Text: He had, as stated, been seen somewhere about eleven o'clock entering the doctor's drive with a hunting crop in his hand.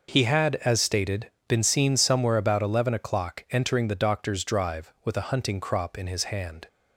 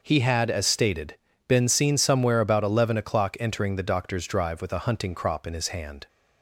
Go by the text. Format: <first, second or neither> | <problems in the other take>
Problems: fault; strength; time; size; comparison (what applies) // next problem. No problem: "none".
neither | none